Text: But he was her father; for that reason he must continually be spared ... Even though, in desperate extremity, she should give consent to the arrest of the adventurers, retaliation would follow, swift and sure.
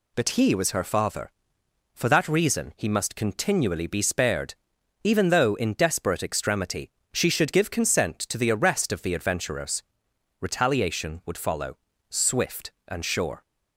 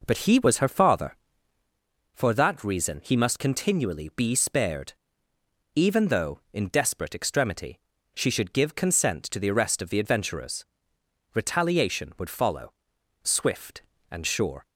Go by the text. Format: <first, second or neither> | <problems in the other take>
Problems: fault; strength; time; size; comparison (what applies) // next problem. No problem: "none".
first | starts louder than the rest; noticeable; until 1.9 s; 5 dB